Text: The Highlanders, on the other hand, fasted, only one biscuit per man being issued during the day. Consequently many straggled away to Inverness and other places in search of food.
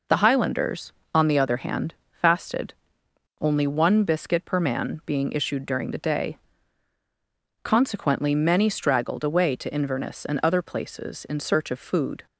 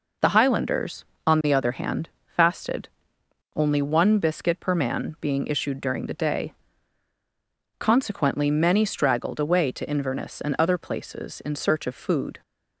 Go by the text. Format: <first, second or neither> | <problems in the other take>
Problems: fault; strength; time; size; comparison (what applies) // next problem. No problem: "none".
neither | none